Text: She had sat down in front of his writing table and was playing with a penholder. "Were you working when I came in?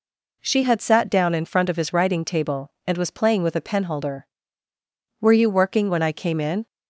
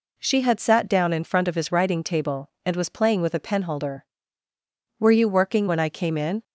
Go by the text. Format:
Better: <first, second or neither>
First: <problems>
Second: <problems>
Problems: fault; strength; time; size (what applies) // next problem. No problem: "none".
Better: neither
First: none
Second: none